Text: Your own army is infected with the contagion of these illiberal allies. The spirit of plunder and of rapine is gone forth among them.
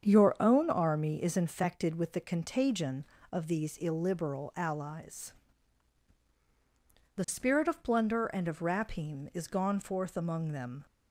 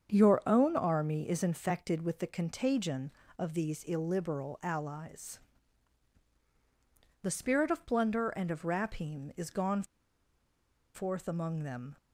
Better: first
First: starts louder than the rest; strong; until 1.0 s; 7.5 dB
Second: starts louder than the rest; strong; until 1.1 s; 7.5 dB // pauses between "gone" and "forth"; at 9.8 s; 1.1 s long

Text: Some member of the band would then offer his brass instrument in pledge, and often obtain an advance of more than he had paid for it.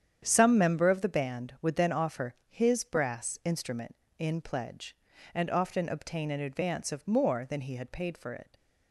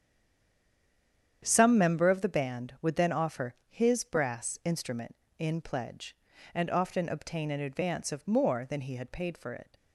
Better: first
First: starts louder than the rest; strong; until 1.2 s; 8.5 dB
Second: stays silent before the first word; noticeable; until 1.4 s; 1.4 s long // starts louder than the rest; strong; until 2.4 s; 8.5 dB

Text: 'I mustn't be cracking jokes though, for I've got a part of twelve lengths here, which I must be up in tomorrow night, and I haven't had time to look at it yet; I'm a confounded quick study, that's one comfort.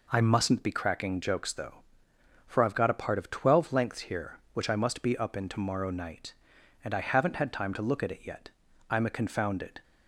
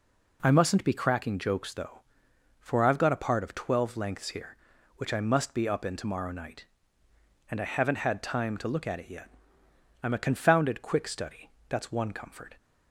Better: second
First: stops before "quick study that's one comfort"; at 9.8 s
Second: none

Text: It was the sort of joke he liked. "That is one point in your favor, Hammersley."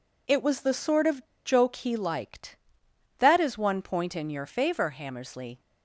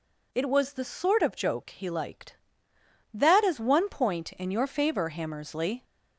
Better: second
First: pauses between "of" and "joke"; slight; at 1.2 s; 0.21 s long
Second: none

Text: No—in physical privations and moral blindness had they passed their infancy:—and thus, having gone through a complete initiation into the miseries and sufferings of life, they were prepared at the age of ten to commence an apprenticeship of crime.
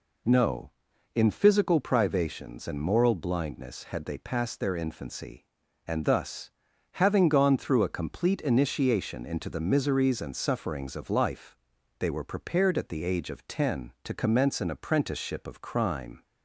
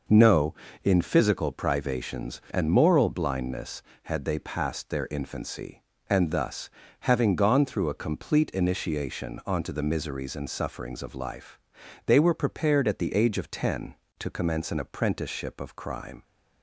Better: first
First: none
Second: says "onto" for "into"; at 9.4 s

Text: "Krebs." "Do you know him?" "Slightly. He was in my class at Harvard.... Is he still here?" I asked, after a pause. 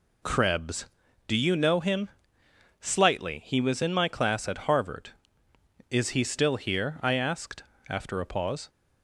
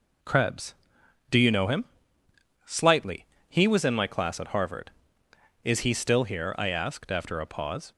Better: neither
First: none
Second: none

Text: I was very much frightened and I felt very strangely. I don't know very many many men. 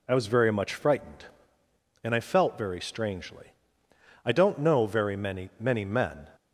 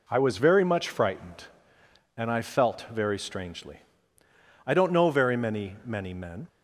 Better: neither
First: none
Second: none

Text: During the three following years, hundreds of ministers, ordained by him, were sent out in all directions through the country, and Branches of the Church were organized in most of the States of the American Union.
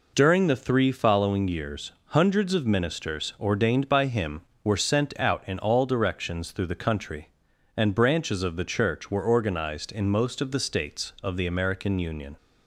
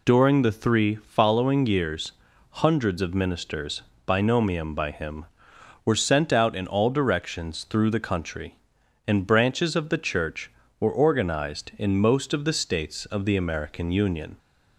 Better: first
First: none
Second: says "binomium" for "ordained"; at 4.0 s

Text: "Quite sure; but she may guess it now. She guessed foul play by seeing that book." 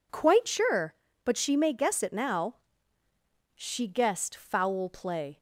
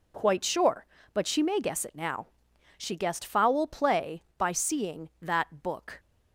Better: second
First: stops before "by seeing that book"; at 5.3 s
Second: none

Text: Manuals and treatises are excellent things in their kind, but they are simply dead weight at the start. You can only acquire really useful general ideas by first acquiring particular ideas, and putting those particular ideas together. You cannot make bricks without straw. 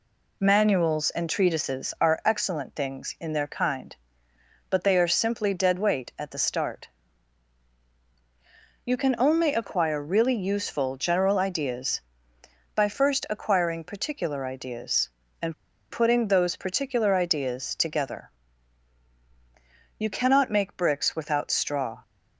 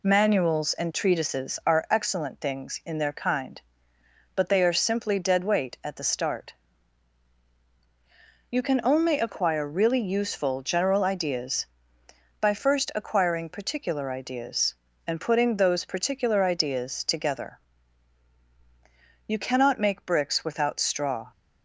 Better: second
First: pauses between "and" and "putting"; at 15.5 s; 0.36 s long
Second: none

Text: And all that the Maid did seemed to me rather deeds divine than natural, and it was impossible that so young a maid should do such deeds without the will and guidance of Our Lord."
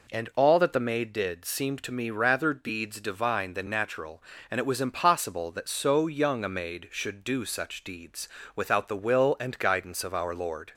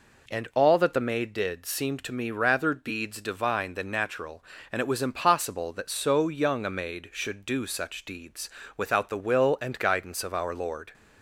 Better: neither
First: pauses between "deeds" and "without"; slight; at 8.2 s; 0.28 s long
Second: pauses between "deeds" and "without"; slight; at 8.4 s; 0.28 s long

